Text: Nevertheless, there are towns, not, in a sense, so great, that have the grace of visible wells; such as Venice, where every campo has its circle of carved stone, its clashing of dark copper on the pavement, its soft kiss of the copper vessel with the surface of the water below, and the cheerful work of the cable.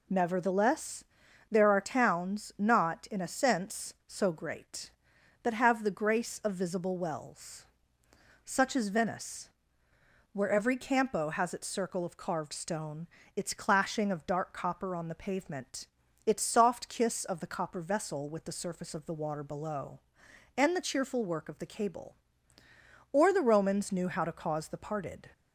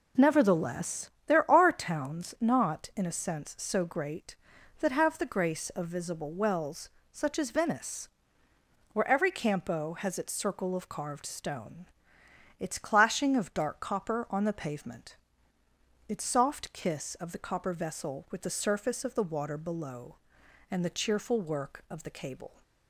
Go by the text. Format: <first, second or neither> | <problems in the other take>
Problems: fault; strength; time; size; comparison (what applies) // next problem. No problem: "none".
second | goes on to say "Or the Romans knew how to cause the parted"; strong; from 23.1 s on; 2.1 s long